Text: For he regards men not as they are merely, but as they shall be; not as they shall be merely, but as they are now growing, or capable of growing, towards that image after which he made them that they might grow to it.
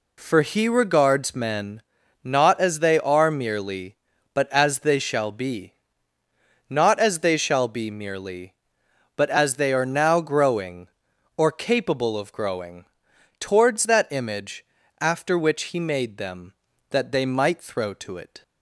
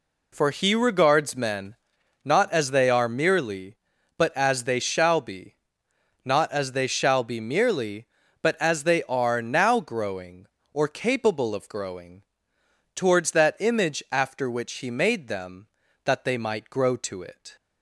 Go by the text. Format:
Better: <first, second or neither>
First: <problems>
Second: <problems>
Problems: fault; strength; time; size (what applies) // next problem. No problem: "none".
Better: second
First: pauses between "men" and "not"; at 1.8 s; 0.44 s long // pauses between "image" and "after"; slight; at 14.6 s; 0.36 s long // says "throw" for "grow"; at 17.6 s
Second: pauses between "men" and "not"; noticeable; at 1.7 s; 0.48 s long